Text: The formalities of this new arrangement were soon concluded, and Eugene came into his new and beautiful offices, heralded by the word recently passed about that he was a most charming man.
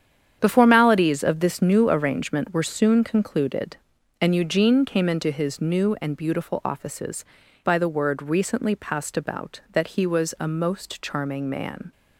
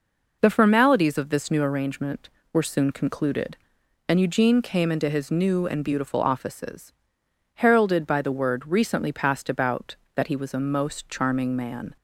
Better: second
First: starts louder than the rest; strong; until 1.4 s; 8.5 dB // skips "heralded"; at 7.4 s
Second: none

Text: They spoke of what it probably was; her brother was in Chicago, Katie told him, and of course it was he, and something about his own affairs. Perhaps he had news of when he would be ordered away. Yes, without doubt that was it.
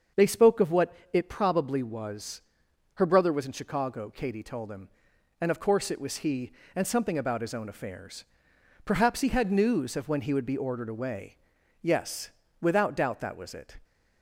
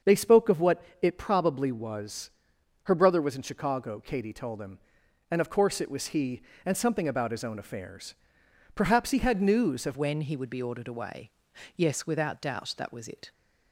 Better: first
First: starts louder than the rest; until 1.3 s; 6.5 dB // pauses between "what" and "it"; slight; at 0.9 s; 0.20 s long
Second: starts louder than the rest; until 1.2 s; 6.5 dB // pauses between "what" and "it"; slight; at 0.8 s; 0.20 s long // changes voice at "when"; from 9.9 s on; 3.4 s long

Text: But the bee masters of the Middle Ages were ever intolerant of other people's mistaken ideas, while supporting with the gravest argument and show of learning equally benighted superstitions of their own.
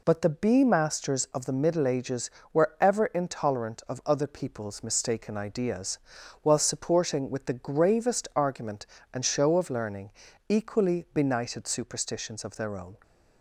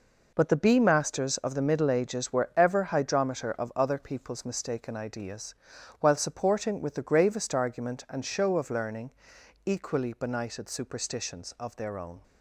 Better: first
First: pauses between "learning" and "equally"; at 10.1 s; 0.38 s long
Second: says "hydrometer" for "intolerant"; at 2.8 s // pauses between "learning" and "equally"; noticeable; at 9.1 s; 0.56 s long

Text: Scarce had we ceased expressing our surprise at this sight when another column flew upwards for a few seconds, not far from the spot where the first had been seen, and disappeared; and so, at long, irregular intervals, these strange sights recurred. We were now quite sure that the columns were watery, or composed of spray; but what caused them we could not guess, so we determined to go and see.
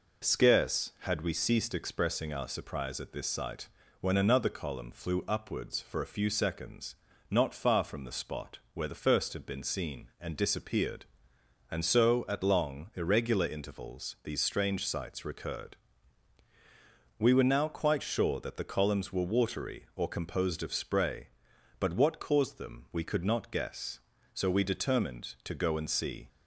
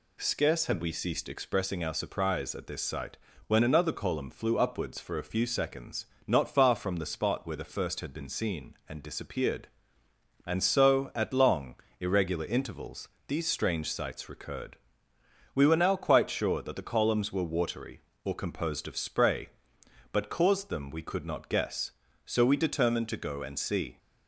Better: first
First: pauses between "sight" and "when"; slight; at 3.6 s; 0.32 s long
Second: pauses between "sight" and "when"; slight; at 3.1 s; 0.28 s long // skips "what"; at 20.2 s

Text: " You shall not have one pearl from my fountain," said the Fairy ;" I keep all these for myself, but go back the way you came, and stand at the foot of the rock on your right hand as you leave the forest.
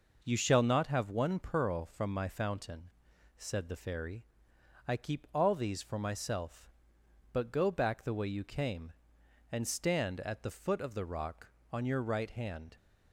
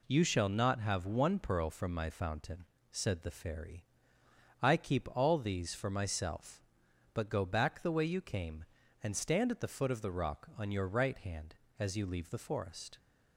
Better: second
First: stops before "as you leave the forest"; at 12.7 s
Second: none

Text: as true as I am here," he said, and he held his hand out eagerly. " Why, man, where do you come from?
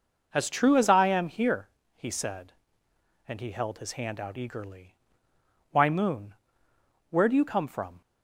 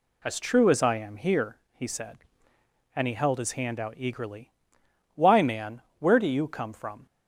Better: second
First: starts louder than the rest; noticeable; until 1.3 s; 6 dB // says "moon" for "man"; at 5.8 s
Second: none

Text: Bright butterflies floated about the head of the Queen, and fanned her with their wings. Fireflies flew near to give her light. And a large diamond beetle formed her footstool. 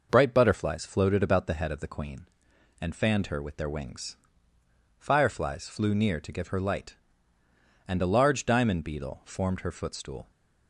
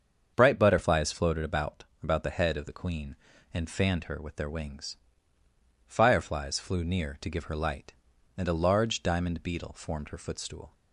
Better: first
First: none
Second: starts louder than the rest; until 1.3 s; 7 dB // says "about" twice; at 2.0 s

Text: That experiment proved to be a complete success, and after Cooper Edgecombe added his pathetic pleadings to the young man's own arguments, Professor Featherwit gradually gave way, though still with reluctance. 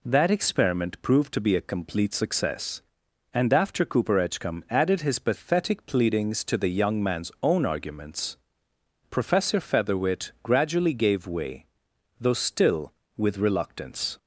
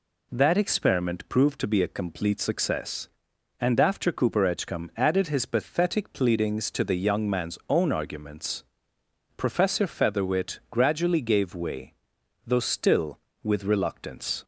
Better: neither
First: none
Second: none

